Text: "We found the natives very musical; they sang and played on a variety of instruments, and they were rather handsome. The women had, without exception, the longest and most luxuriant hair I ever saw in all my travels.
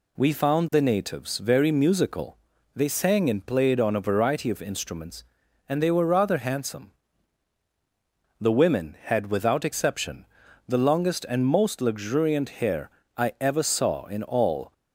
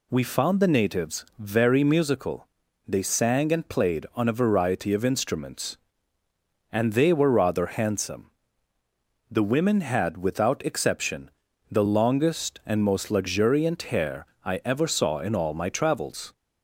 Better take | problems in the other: second | pauses between "hair" and "I"; slight; at 12.9 s; 0.26 s long; slight in the second // stops before "my travels"; at 14.7 s

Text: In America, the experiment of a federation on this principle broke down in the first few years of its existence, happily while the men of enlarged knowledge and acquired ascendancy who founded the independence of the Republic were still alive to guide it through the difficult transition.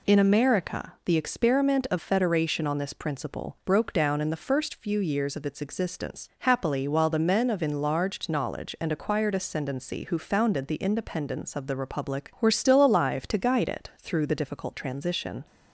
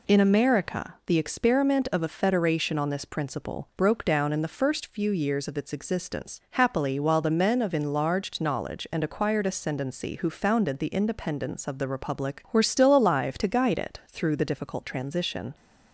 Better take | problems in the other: second | skips "a"; at 1.9 s

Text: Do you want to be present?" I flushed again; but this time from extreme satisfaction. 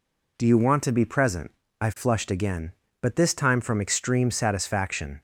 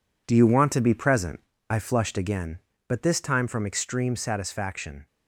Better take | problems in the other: first | gets quieter; strong; throughout; 8.5 dB

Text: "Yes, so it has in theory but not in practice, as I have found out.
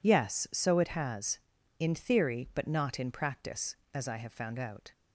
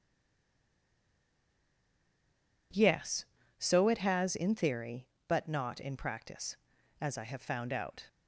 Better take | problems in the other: first | stays silent before the first word; strong; until 2.7 s; 2.7 s long

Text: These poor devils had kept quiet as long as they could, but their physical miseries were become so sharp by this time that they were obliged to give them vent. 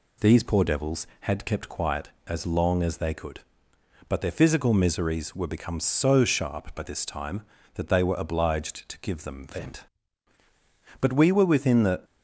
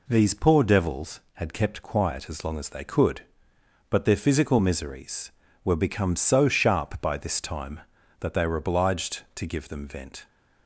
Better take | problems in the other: second | goes on to say "But we were within the"; noticeable; from 11.0 s on; 1.0 s long

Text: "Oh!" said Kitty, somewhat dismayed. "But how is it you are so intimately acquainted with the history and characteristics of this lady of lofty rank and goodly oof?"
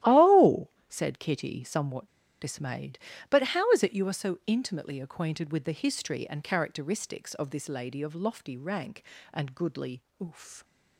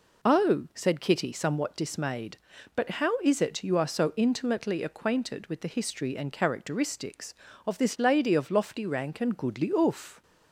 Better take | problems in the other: second | starts louder than the rest; strong; until 1.2 s; 14 dB // pauses between "somewhat" and "dismayed"; slight; at 2.0 s; 0.32 s long // pauses between "goodly" and "oof"; slight; at 10.0 s; 0.18 s long

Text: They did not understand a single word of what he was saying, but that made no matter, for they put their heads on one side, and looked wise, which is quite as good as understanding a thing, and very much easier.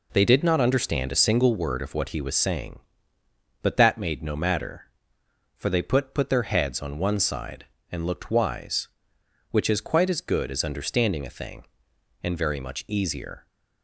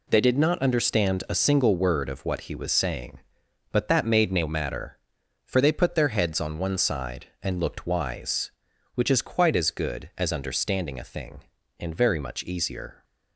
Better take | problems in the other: second | says "put" twice; at 6.1 s

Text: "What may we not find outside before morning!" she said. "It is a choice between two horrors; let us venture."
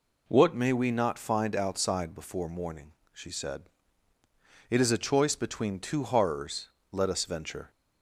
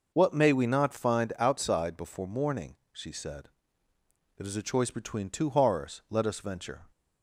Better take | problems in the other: neither | none

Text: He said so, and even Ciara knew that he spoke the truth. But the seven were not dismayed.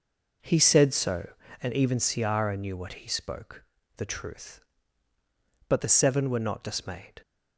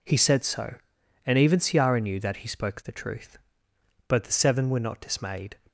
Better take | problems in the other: second | says "what" for "that"; at 2.7 s // pauses between "spoke" and "the"; slight; at 3.6 s; 0.32 s long

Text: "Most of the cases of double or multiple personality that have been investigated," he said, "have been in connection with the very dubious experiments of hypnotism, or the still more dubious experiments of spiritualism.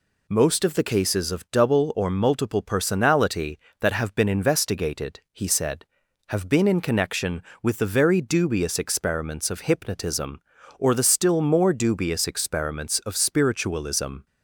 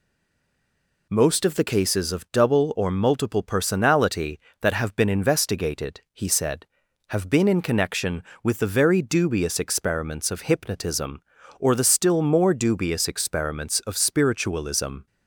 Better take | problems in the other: first | stays silent before the first word; until 1.0 s; 1.0 s long

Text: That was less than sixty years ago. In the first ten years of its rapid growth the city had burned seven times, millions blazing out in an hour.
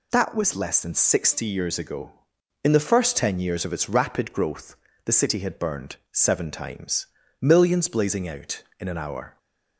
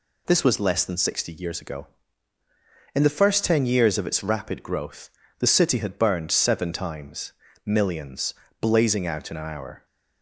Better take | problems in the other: first | says "This" for "That"; at 0.2 s // pauses between "growth" and "the"; slight; at 5.1 s; 0.26 s long; slight in the first // pauses between "millions" and "blazing"; slight; at 8.3 s; 0.26 s long

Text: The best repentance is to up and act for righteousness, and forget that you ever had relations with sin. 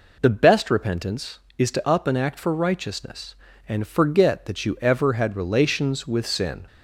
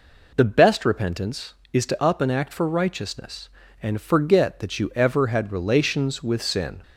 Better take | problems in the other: neither | none

